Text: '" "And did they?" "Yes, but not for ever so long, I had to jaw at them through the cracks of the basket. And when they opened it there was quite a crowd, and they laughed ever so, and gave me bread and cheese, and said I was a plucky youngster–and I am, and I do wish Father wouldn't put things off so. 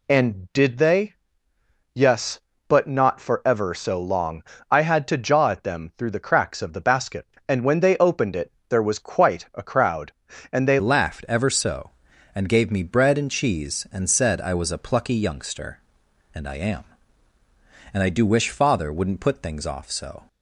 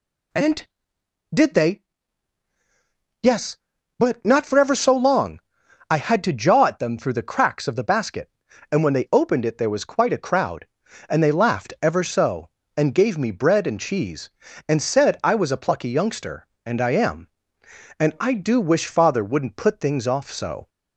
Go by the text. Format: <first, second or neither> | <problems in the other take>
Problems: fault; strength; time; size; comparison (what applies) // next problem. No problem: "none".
second | pauses between "it" and "there"; slight; at 8.5 s; 0.18 s long // changes voice at "laughed"; from 10.7 s on; 9.5 s long